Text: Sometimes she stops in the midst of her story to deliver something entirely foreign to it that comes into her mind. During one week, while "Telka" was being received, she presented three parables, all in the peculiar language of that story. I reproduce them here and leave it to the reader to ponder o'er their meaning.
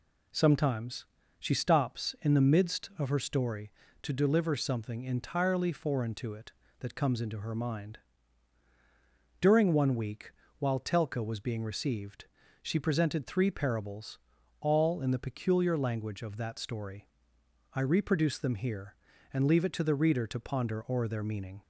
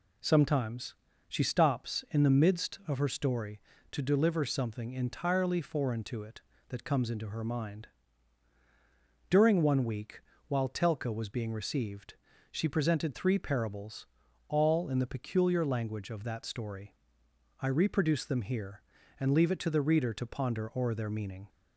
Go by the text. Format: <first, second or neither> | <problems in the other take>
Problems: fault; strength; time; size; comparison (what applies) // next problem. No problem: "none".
neither | pauses between "Sometimes" and "she"; slight; the same in both